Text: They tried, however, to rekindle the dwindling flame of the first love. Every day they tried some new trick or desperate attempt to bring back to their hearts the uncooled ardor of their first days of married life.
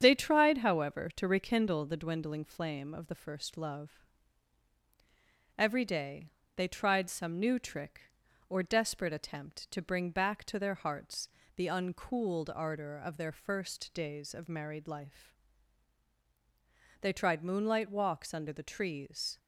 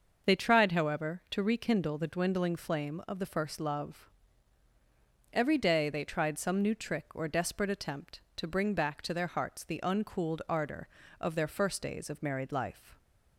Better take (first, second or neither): second